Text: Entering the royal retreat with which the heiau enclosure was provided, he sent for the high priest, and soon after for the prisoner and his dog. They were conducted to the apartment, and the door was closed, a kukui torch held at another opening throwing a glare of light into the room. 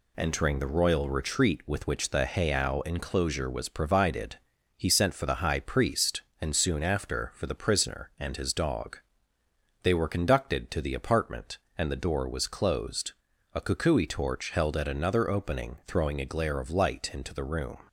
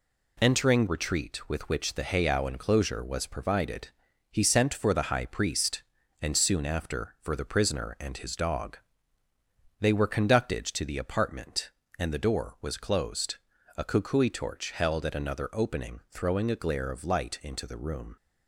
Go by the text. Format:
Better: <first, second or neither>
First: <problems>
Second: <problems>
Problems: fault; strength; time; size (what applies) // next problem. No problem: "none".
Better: first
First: none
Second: skips "the royal"; at 0.8 s